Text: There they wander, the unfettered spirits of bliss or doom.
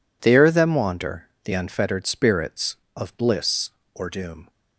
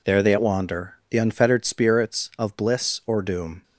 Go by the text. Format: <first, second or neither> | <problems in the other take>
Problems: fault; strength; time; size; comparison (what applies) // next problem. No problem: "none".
second | says "them" for "they"; at 0.5 s